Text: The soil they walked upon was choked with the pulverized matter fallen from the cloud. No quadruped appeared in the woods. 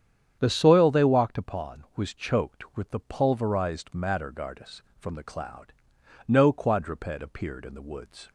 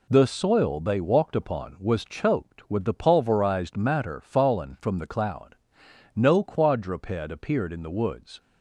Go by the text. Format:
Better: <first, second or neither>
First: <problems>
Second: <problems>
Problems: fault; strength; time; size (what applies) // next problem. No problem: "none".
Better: second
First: starts louder than the rest; strong; until 1.4 s; 8.5 dB // says "gardus" for "fallen"; at 4.3 s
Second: none